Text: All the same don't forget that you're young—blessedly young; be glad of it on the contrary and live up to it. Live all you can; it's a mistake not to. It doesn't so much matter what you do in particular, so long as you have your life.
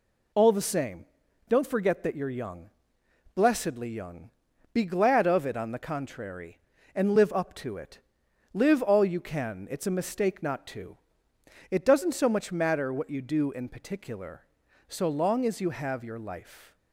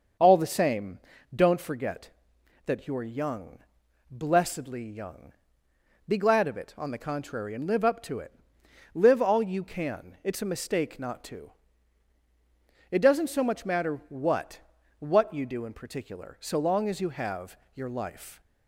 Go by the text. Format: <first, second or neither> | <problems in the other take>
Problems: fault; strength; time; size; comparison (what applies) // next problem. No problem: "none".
first | starts louder than the rest; until 1.5 s; 6.5 dB // pauses between "same" and "don't"; slight; at 0.9 s; 0.36 s long; also in the first // says "what" twice; at 15.0 s // pauses between "have" and "your"; slight; at 17.5 s; 0.16 s long